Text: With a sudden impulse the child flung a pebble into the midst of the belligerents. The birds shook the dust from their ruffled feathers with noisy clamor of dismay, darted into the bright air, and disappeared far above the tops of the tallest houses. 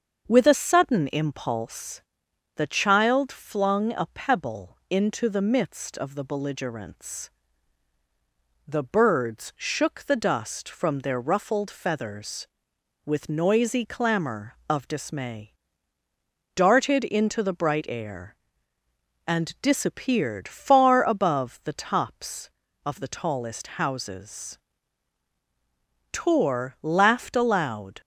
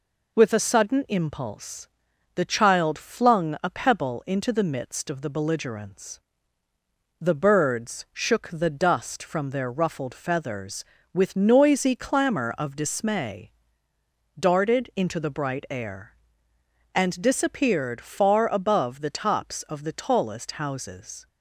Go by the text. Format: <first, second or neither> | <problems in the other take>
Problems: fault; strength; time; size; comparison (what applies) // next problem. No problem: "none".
second | starts louder than the rest; until 1.3 s; 6.5 dB // pauses between "impulse" and "the"; noticeable; at 2.0 s; 0.54 s long; also in the second // goes on to say "Tor laughed aloud"; strong; from 26.1 s on; 1.9 s long